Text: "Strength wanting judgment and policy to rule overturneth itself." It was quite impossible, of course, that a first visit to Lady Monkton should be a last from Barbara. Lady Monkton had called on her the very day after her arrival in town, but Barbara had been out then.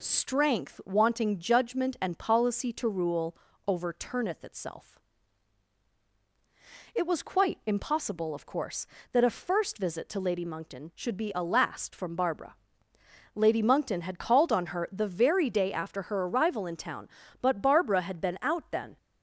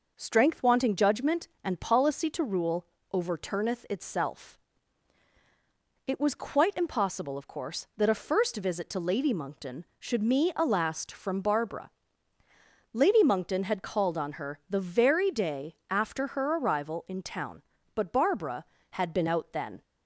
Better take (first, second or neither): first